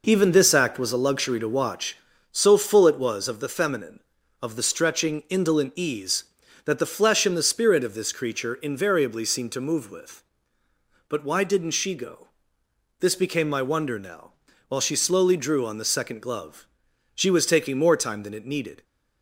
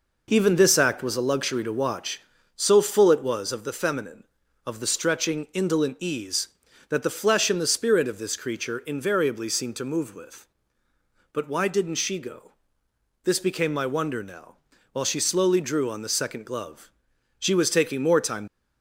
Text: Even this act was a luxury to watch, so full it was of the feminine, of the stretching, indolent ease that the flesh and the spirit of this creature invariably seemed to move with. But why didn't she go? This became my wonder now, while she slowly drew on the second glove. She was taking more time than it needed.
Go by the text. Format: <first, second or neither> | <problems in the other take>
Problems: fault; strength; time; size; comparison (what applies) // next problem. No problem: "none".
first | stops before "than it needed"; at 18.4 s